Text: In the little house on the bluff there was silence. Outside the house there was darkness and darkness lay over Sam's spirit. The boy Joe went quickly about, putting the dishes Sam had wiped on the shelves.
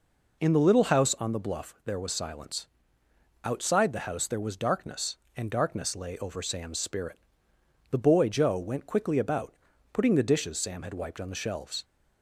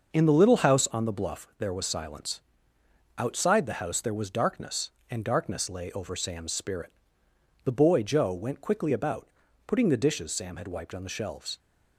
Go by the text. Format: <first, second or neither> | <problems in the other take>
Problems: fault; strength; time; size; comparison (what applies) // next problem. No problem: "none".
first | gets quieter; strong; throughout; 7.5 dB